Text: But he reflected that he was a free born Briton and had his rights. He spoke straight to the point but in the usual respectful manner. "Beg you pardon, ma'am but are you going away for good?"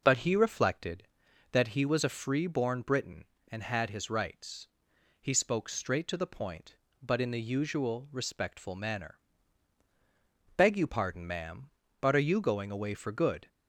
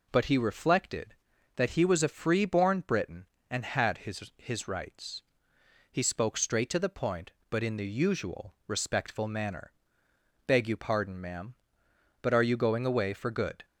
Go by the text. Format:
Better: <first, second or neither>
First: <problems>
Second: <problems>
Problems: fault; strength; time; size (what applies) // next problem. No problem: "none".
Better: first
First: none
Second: says "his" twice; at 4.3 s